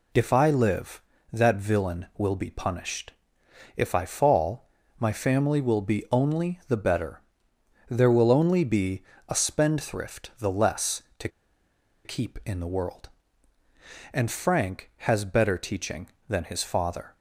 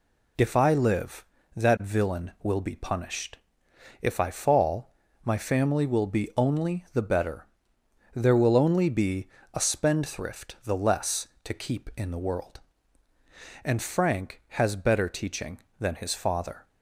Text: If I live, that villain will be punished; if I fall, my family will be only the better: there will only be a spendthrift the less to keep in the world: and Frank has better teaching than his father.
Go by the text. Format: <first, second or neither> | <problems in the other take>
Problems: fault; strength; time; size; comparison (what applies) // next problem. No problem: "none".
second | pauses between "be" and "a"; slight; at 9.0 s; 0.26 s long; slight in the second // pauses between "to" and "keep"; noticeable; at 11.2 s; 0.75 s long